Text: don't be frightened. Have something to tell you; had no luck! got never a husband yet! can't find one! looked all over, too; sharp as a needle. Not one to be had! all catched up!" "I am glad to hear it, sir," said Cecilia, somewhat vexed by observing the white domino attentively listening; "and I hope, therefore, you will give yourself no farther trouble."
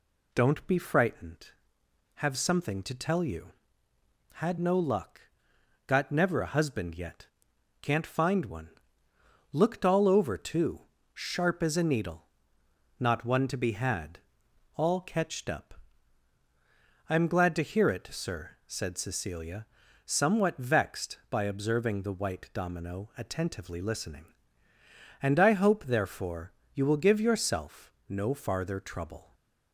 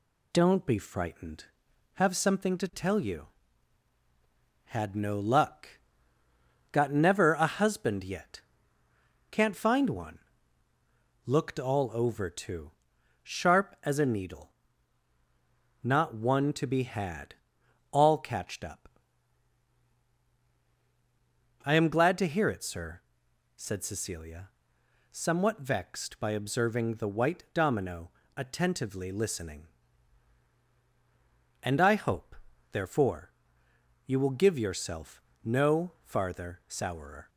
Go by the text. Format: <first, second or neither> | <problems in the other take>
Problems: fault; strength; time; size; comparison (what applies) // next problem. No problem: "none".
first | pauses between "domino" and "attentively"; slight; at 28.1 s; 0.24 s long // pauses between "yourself" and "no"; slight; at 35.2 s; 0.20 s long; slight in the first // says "sourer" for "trouble"; at 36.6 s